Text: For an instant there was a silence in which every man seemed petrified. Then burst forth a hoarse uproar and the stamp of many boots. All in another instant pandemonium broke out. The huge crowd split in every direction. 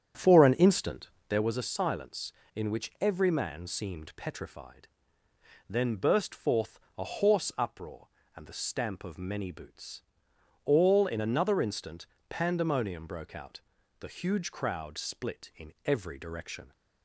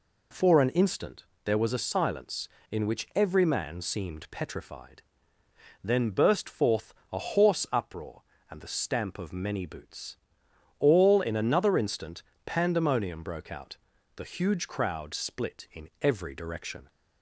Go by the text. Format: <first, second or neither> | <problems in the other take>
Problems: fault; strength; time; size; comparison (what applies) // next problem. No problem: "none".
second | starts louder than the rest; strong; until 1.5 s; 9 dB // pauses between "instant" and "there"; slight; at 1.0 s; 0.18 s long; slight in the second // pauses between "forth" and "a"; slight; at 6.7 s; 0.18 s long; slight in the second // pauses between "instant" and "pandemonium"; slight; at 12.0 s; 0.22 s long; slight in the second